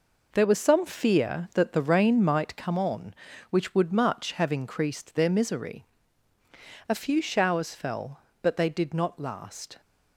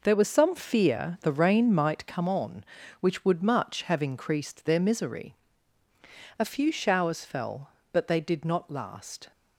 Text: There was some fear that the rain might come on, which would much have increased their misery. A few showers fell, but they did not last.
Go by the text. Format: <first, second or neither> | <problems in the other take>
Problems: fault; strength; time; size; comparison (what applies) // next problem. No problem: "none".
first | skips "that"; at 1.2 s